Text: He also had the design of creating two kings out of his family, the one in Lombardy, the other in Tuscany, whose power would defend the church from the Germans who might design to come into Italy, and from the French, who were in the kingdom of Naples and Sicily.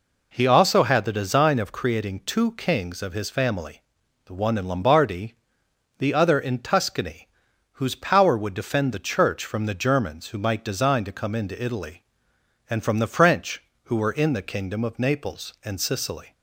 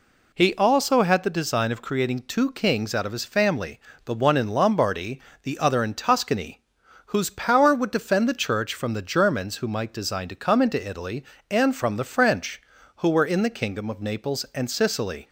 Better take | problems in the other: second | skips "out"; at 3.0 s

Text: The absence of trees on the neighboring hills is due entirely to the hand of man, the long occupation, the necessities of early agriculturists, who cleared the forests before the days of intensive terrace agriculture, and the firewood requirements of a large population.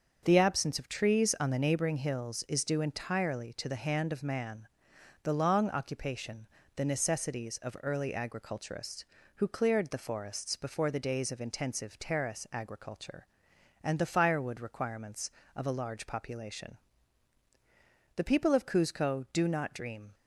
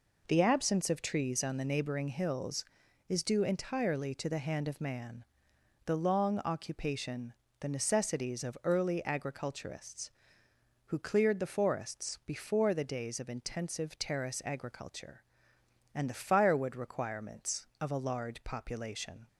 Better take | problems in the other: second | starts louder than the rest; until 1.2 s; 6.5 dB // goes on to say "The people of Cuzco do not dream"; strong; from 18.1 s on; 1.9 s long

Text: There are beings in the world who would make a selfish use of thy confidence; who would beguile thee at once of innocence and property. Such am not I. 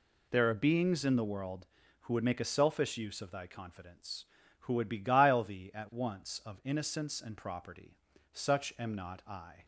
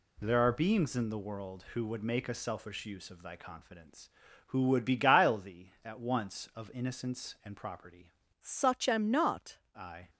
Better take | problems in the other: first | changes voice from "Such" to "not"; from 8.3 to 9.5 s; 1.2 s long

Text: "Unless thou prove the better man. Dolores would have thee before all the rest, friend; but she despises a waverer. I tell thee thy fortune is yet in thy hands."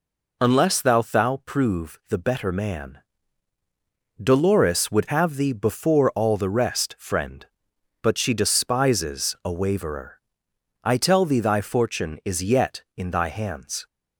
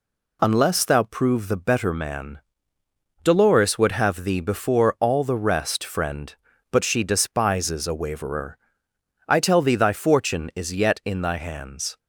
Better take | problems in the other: second | says "thou" twice; at 0.9 s

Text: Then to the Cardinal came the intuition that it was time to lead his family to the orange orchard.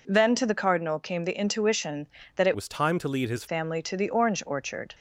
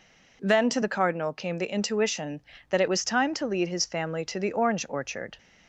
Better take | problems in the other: second | changes voice from "was" to "his"; from 2.5 to 3.4 s; 0.9 s long

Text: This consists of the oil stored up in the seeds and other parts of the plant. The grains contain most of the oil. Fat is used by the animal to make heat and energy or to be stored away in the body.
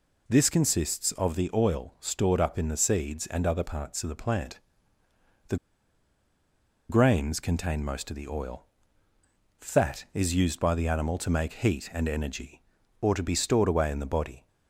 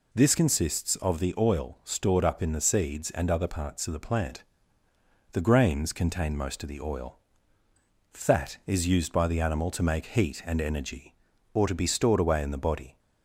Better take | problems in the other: second | pauses between "The" and "grains"; strong; at 5.5 s; 1.3 s long

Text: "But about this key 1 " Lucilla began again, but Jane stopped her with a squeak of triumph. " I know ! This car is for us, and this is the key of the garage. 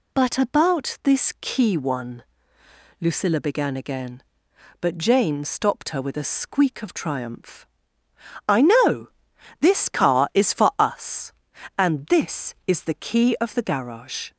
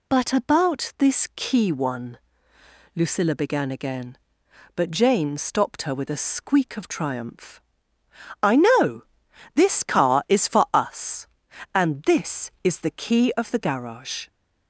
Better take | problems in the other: neither | none

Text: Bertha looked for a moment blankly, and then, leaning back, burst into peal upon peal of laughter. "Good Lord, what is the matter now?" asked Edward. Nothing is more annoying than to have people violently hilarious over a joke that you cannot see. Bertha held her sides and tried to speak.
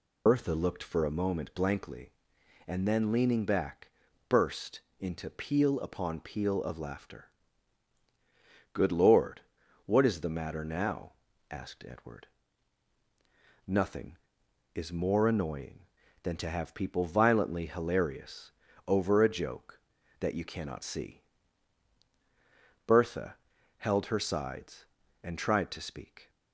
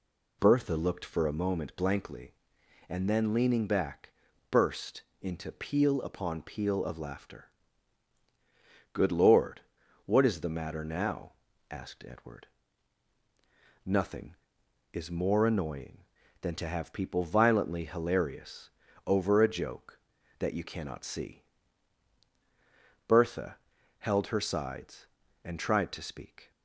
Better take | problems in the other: second | loses the start of "Bertha"; at 0.2 s; 75 ms // pauses between "burst" and "into"; slight; at 4.8 s; 0.18 s long; slight in the second // pauses between "hilarious" and "over"; at 18.5 s; 0.37 s long; also in the second // pauses between "Bertha" and "held"; at 23.3 s; 0.42 s long; also in the second

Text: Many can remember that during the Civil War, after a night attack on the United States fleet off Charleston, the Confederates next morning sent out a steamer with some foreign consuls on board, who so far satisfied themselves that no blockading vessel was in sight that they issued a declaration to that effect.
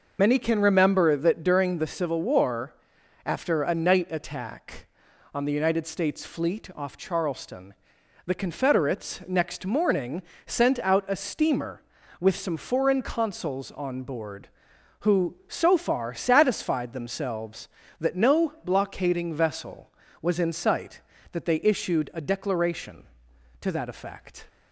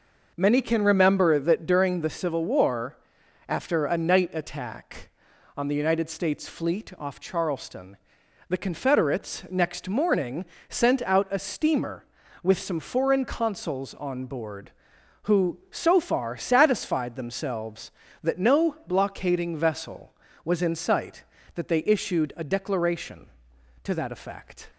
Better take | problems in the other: second | loses the start of "Many"; at 0.1 s; 70 ms // pauses between "morning" and "sent"; slight; at 10.2 s; 0.24 s long; slight in the second

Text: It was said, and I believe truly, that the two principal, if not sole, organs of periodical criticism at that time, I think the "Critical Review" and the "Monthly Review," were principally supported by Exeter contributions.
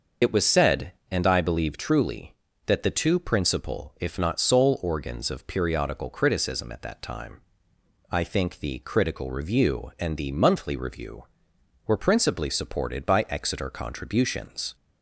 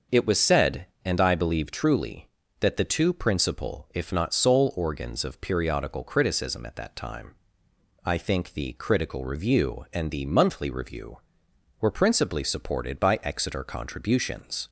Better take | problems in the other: second | loses the start of "It"; at 0.2 s; 50 ms // starts louder than the rest; until 1.4 s; 6.5 dB; also in the second

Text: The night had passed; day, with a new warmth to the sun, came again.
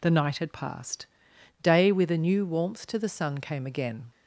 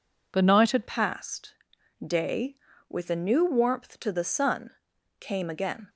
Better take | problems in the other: first | changes voice at "passed"; from 0.8 s on; 5.0 s long

